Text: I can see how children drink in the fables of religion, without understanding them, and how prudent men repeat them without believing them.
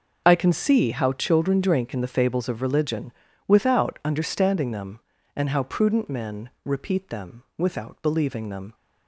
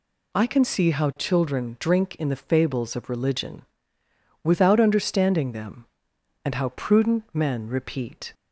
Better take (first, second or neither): first